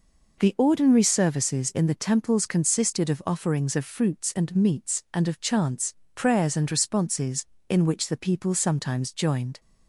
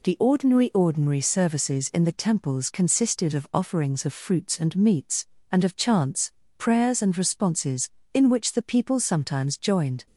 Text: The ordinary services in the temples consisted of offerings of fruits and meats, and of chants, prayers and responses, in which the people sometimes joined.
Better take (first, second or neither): first